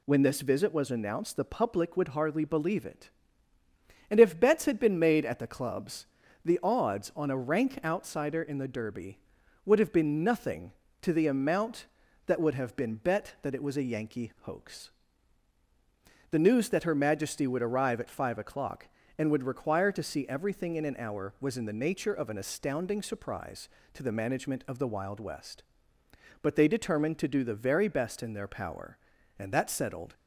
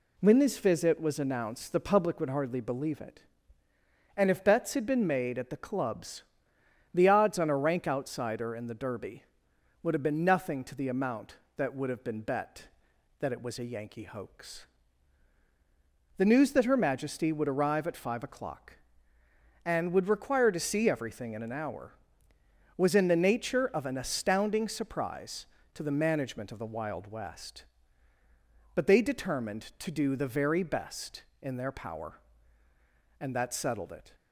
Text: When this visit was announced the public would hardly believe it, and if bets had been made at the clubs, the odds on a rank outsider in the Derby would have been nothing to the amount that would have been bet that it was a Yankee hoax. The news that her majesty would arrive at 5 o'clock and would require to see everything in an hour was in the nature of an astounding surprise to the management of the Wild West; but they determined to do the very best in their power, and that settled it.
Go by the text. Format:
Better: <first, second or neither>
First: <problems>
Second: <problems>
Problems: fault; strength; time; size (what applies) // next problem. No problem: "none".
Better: second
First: stops before "it"; at 30.1 s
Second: none